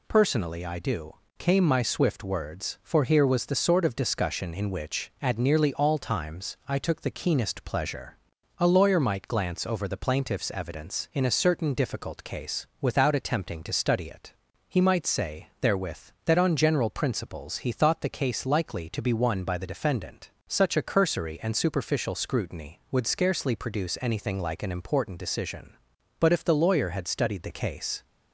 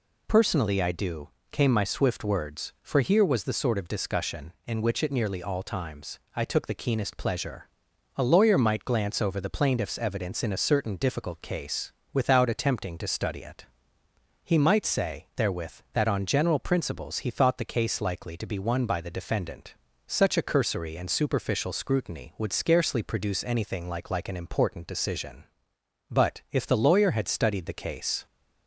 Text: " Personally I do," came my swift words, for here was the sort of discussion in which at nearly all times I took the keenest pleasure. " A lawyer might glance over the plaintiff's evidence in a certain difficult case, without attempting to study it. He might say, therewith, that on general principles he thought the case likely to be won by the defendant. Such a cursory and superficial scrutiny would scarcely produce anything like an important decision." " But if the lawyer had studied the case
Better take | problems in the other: first | pauses between "times" and "I"; slight; at 6.1 s; 0.18 s long // says "like" twice; at 24.0 s

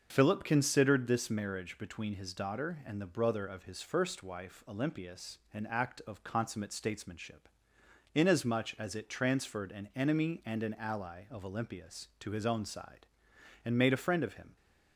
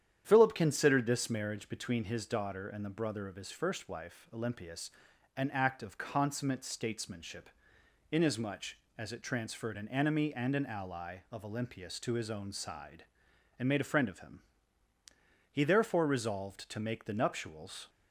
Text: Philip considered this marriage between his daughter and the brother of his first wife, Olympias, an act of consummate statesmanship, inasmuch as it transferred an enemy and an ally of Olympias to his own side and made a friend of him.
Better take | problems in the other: first | starts louder than the rest; strong; until 1.2 s; 9.5 dB; also in the first // goes on to say "He therefore resolved to make the nuptials"; strong; from 15.5 s on; 2.3 s long

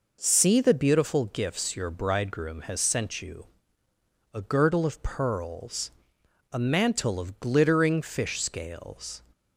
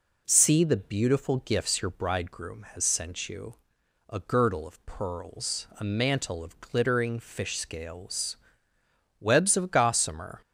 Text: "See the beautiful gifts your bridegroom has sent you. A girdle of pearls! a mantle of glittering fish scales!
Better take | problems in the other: first | goes on to say "webs of gossamer"; noticeable; from 9.2 s on; 1.2 s long

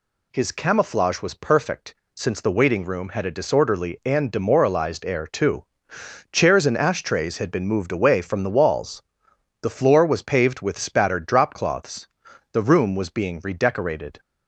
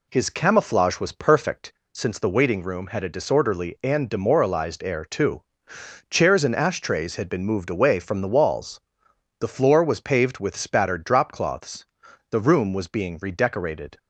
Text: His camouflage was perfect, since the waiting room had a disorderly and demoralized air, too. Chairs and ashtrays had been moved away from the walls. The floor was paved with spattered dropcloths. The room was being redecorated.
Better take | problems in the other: first | starts louder than the rest; slight; until 1.9 s; 2 dB

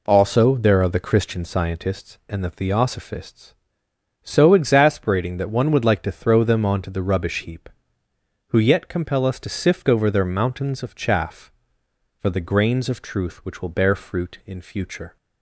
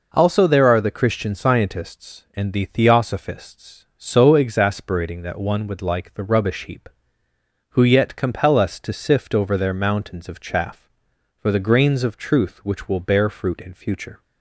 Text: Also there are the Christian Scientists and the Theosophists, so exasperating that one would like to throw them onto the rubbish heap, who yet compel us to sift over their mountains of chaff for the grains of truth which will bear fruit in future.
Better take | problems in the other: first | skips "to throw them onto"; at 6.1 s

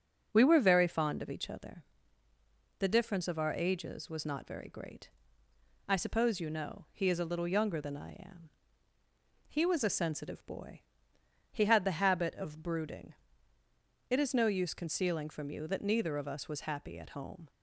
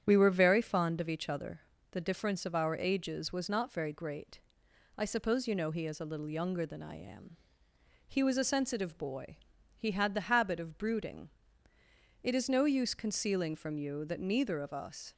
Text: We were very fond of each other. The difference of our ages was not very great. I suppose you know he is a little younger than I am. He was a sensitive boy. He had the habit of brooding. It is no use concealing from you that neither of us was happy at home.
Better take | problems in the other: first | starts louder than the rest; strong; until 1.0 s; 9 dB; also in the first // stops before "was happy at home"; at 15.1 s

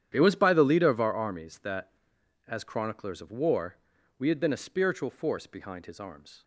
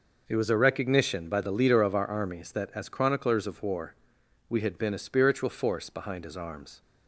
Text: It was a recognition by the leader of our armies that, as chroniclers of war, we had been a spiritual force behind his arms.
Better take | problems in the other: second | starts louder than the rest; strong; until 1.1 s; 10 dB // skips "a recognition"; at 0.3 s

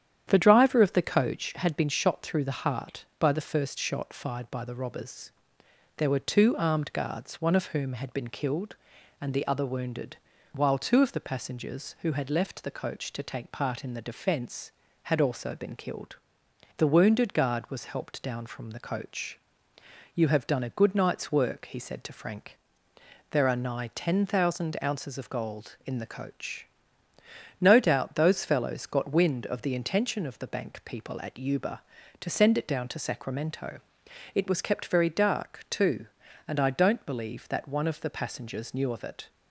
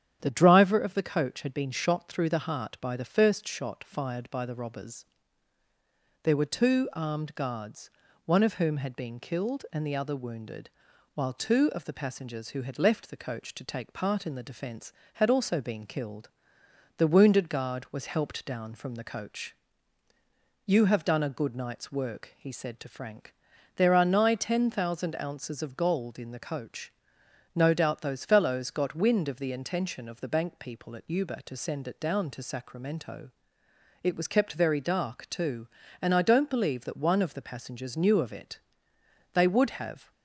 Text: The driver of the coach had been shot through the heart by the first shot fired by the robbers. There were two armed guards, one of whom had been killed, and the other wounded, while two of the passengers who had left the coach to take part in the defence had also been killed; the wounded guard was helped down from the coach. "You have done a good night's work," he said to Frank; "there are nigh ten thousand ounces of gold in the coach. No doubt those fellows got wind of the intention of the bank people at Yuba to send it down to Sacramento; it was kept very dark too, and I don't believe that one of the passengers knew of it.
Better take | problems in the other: first | starts louder than the rest; strong; until 1.2 s; 9.5 dB; strong in the first // goes on to say "They would have"; noticeable; from 39.3 s on; 0.78 s long

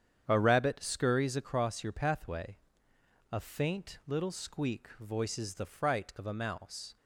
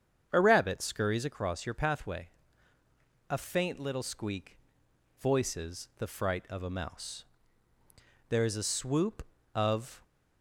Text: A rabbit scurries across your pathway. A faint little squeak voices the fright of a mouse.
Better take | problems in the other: first | starts louder than the rest; strong; until 1.3 s; 7.5 dB; strong in the first // pauses between "squeak" and "voices"; noticeable; at 4.5 s; 0.62 s long // goes on to say "There is a swoop of"; strong; from 8.2 s on; 1.7 s long

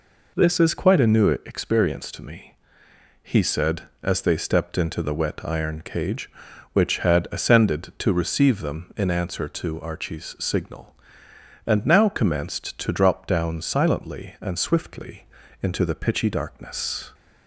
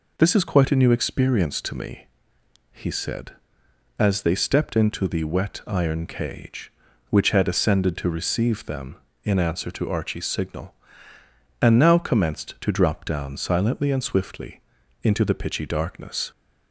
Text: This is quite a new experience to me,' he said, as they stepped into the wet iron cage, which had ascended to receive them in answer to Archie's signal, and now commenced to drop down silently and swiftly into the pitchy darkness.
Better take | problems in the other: neither | pauses between "swiftly" and "into"; the same in both

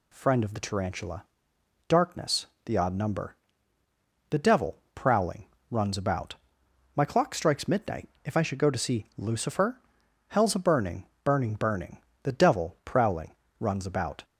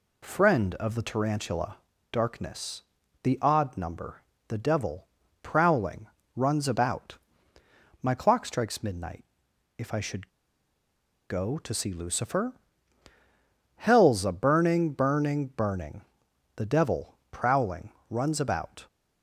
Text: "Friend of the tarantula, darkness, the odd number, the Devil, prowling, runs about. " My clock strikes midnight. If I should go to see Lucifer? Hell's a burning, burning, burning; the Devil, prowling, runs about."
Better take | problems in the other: first | pauses between "should" and "go"; at 10.2 s; 0.99 s long

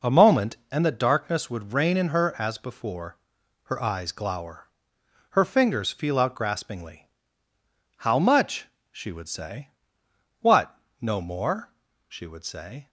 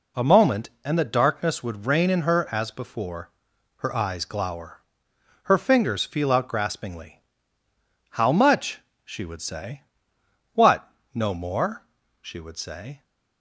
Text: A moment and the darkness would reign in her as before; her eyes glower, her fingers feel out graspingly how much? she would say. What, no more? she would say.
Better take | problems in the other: second | starts louder than the rest; noticeable; until 1.0 s; 5 dB // pauses between "graspingly" and "how"; noticeable; at 7.0 s; 0.90 s long; noticeable in the second

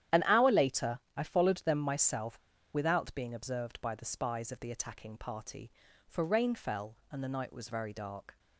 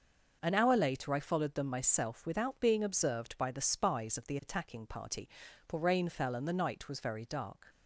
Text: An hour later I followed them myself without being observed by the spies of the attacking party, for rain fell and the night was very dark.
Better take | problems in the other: second | starts louder than the rest; strong; until 1.2 s; 11 dB // pauses between "later" and "I"; slight; at 1.0 s; 0.16 s long // pauses between "myself" and "without"; slight; at 2.3 s; 0.35 s long

